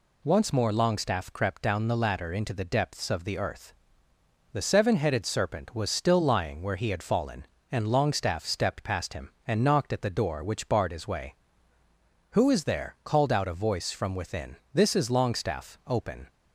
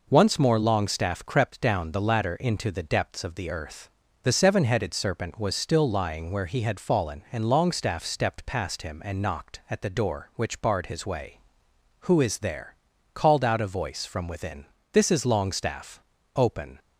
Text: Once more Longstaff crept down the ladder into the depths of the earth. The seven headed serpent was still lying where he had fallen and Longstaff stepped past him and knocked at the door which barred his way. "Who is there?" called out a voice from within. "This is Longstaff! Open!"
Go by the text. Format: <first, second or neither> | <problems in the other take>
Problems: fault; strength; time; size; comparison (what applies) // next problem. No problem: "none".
neither | none